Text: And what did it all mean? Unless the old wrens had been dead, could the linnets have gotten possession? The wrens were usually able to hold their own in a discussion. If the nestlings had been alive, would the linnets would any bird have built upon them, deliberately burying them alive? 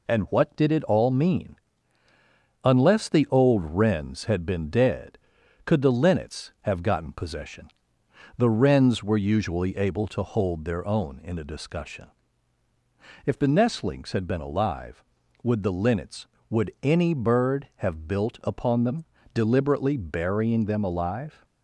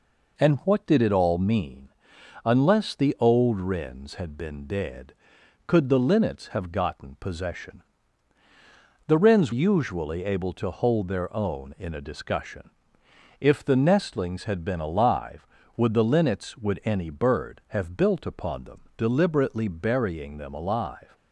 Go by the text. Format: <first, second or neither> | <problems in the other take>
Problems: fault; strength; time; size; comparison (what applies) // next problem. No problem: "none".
first | skips "were"; at 9.5 s